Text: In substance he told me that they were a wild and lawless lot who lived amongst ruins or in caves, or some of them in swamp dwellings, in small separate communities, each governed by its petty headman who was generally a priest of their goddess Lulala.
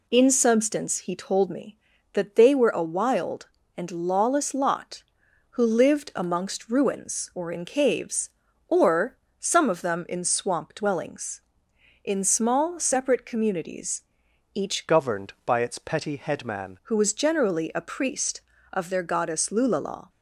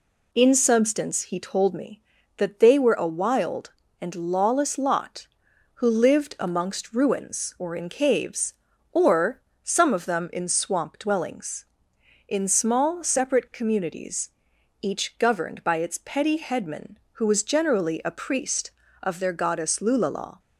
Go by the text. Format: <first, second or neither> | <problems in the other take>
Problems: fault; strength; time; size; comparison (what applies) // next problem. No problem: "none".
second | pauses between "or" and "some"; slight; at 9.1 s; 0.22 s long; slight in the second // changes voice from "governed" to "headman"; from 14.8 to 16.7 s; 1.9 s long